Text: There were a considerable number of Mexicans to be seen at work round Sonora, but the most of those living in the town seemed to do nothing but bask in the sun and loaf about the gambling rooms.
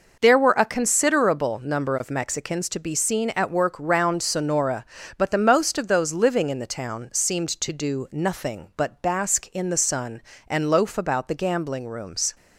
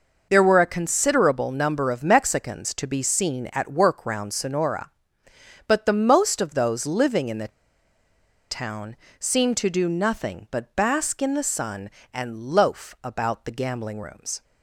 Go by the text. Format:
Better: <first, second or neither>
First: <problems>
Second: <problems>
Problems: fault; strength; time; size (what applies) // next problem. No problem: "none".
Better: first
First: none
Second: pauses between "the" and "town"; at 7.4 s; 1.0 s long // pauses between "town" and "seemed"; slight; at 8.9 s; 0.22 s long